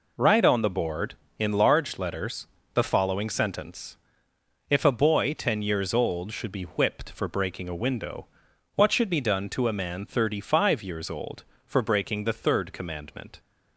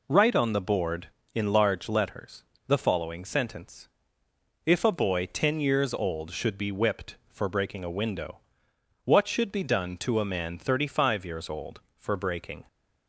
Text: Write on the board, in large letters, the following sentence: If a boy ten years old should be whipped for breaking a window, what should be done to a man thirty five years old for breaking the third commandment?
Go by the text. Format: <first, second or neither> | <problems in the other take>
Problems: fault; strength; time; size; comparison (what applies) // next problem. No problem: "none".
first | stops before "the third commandment"; at 12.6 s